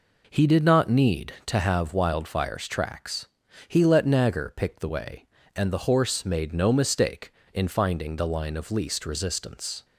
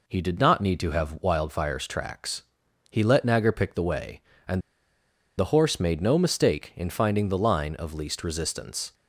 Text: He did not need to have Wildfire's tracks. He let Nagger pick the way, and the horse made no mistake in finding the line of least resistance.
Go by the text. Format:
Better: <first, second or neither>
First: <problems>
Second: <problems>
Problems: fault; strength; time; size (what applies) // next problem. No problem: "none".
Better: first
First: none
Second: pauses between "and" and "the"; noticeable; at 4.6 s; 0.78 s long